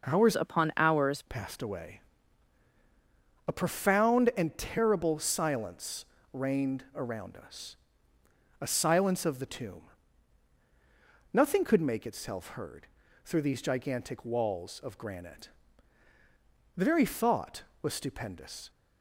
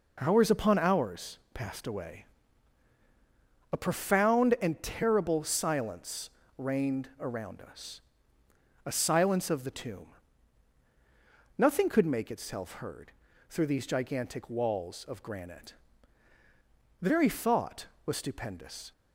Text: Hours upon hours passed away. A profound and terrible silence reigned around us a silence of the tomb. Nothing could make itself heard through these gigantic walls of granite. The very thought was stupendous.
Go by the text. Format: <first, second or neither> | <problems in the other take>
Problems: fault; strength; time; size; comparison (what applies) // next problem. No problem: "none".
second | changes voice from "upon" to "hours"; from 0.3 to 1.2 s; 0.9 s long // pauses between "silence" and "reigned"; slight; at 6.0 s; 0.28 s long; slight in the second // pauses between "us" and "a"; noticeable; at 7.7 s; 0.84 s long; noticeable in the second // pauses between "heard" and "through"; at 12.8 s; 0.38 s long; also in the second